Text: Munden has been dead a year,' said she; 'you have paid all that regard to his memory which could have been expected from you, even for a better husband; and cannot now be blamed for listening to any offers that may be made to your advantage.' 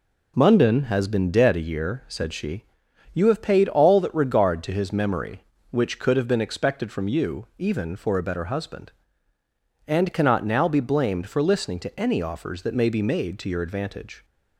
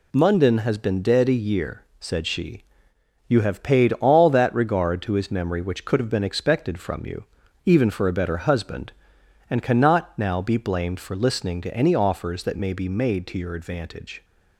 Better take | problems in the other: neither | none

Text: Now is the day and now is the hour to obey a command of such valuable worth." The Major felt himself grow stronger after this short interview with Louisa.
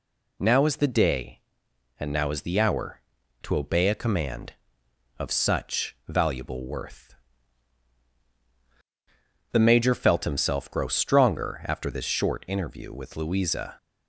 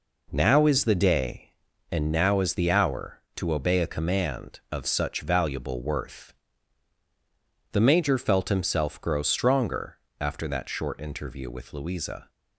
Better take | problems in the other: first | pauses between "stronger" and "after"; slight; at 9.9 s; 0.24 s long // says "that" for "this"; at 10.4 s

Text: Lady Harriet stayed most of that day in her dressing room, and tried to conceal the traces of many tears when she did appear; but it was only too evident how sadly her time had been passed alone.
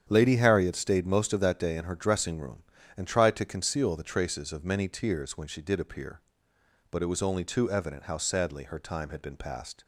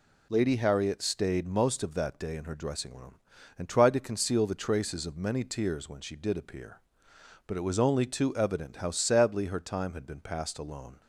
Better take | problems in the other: second | starts louder than the rest; strong; until 1.1 s; 8.5 dB // stops before "alone"; at 9.8 s

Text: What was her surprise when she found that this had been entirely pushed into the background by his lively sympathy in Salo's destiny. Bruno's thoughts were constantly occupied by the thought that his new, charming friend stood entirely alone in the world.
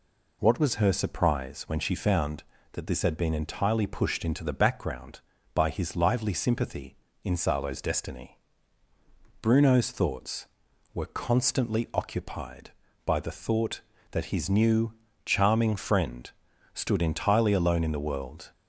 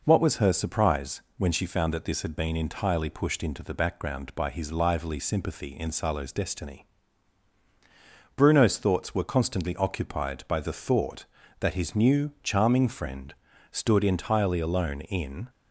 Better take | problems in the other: first | pauses between "surprise" and "when"; slight; at 1.2 s; 0.16 s long // pauses between "friend" and "stood"; at 13.3 s; 0.38 s long; also in the first // stops before "the world"; at 15.4 s

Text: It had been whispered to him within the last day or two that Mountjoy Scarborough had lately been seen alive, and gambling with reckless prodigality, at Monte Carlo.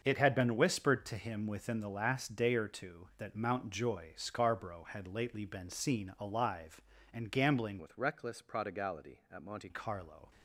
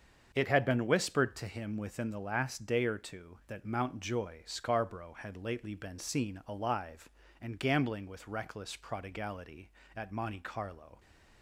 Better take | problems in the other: second | starts louder than the rest; until 1.0 s; 6.5 dB; also in the second // changes voice from "with" to "Monte"; from 7.7 to 9.6 s; 1.9 s long

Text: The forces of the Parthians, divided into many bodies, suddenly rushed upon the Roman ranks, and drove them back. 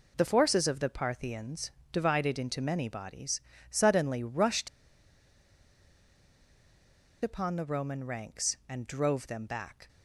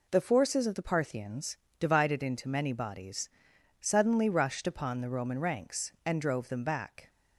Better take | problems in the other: second | pauses between "rushed" and "upon"; strong; at 4.6 s; 2.5 s long

